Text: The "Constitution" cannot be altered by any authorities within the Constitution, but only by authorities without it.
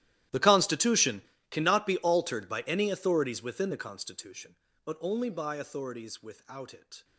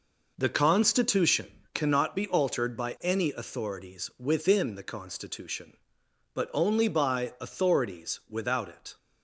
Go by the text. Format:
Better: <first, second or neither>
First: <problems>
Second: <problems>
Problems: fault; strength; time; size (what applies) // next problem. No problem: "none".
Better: second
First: gets quieter; strong; throughout; 21.5 dB // pauses between "Constitution" and "cannot"; slight; at 1.2 s; 0.26 s long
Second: pauses between "Constitution" and "cannot"; slight; at 1.4 s; 0.24 s long